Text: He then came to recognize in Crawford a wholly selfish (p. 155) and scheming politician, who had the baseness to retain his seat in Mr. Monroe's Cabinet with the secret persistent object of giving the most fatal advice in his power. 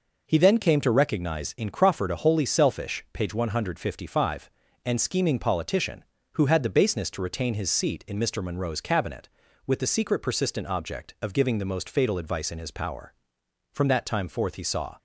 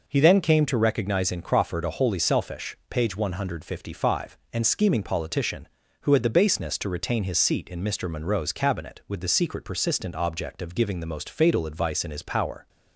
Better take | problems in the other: second | goes on to say "From that time forth he saw"; noticeable; from 13.7 s on; 1.2 s long

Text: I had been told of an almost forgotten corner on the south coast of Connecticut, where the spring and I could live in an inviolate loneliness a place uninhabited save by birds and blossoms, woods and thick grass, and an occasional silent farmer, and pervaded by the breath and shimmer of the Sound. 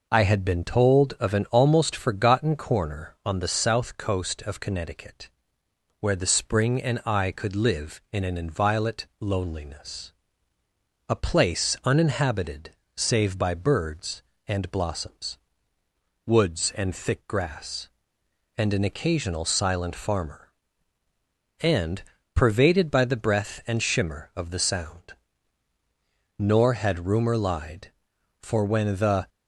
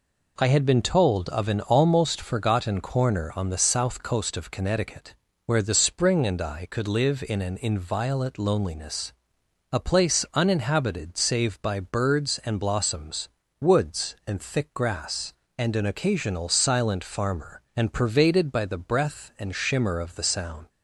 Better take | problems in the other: second | pauses between "loneliness" and "a"; noticeable; at 10.1 s; 0.98 s long; noticeable in the second // pauses between "uninhabited" and "save"; slight; at 12.7 s; 0.24 s long // pauses between "and" and "pervaded"; slight; at 22.0 s; 0.32 s long // goes on to say "Nor had rumor lied for when the"; strong; from 26.3 s on; 2.9 s long

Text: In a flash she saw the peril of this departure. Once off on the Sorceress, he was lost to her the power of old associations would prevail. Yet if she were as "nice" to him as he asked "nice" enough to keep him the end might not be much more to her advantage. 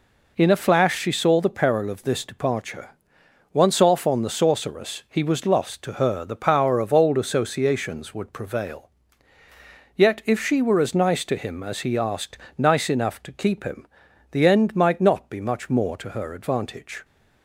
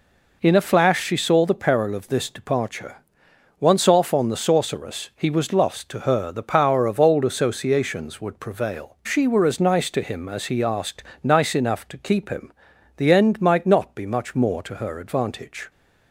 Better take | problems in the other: first | skips "Yet if"; at 9.0 s // pauses between "asked" and "nice"; slight; at 11.0 s; 0.18 s long; slight in the first // pauses between "him" and "the"; at 12.5 s; 0.44 s long; also in the first

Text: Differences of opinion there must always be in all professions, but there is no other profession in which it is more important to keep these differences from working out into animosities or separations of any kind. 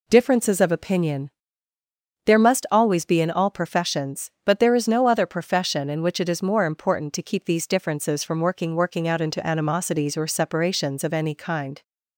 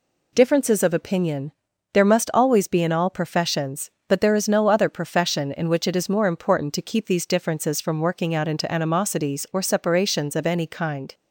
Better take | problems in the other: second | pauses between "opinion" and "there"; noticeable; at 1.3 s; 0.96 s long; also in the second // says "working" twice; at 8.7 s

